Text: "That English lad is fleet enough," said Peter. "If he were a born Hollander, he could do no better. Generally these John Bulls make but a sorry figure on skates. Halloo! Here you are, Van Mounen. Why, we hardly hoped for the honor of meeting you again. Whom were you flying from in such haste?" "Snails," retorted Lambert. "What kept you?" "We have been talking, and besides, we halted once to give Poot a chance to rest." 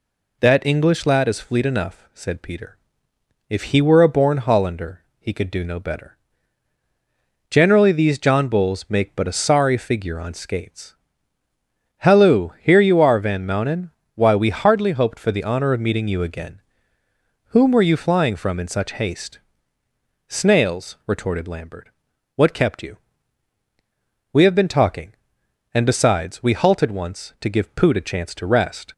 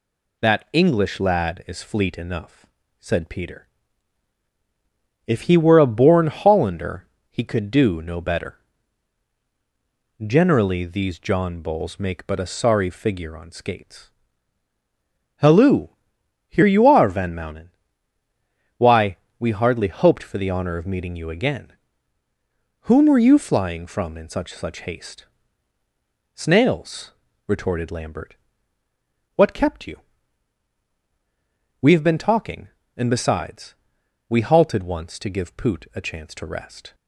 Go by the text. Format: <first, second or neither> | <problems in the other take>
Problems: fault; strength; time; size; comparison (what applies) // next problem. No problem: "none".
first | says "such" twice; at 24.5 s